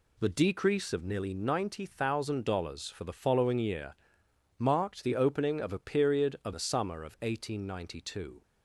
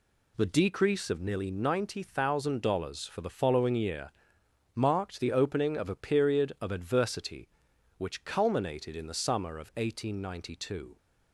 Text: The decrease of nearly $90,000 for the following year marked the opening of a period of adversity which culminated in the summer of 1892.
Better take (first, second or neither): second